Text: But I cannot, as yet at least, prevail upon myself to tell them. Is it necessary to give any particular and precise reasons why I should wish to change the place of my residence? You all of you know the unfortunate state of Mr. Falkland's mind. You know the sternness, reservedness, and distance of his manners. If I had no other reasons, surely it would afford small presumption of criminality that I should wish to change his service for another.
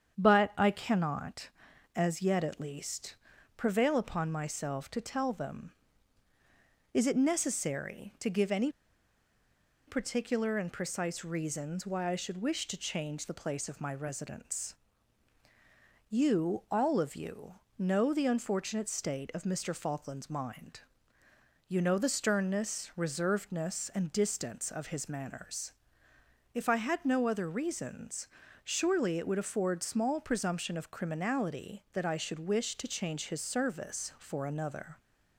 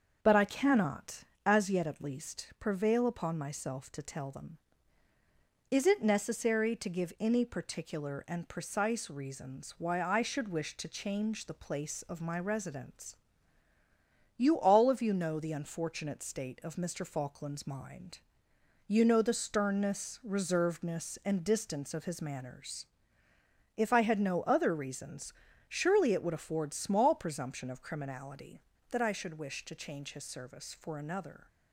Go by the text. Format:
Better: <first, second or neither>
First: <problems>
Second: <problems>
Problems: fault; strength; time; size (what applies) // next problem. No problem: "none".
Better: second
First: starts louder than the rest; strong; until 1.2 s; 8 dB // pauses between "any" and "particular"; at 8.7 s; 1.1 s long // pauses between "you" and "know"; slight; at 17.5 s; 0.24 s long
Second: starts louder than the rest; until 1.2 s; 6.5 dB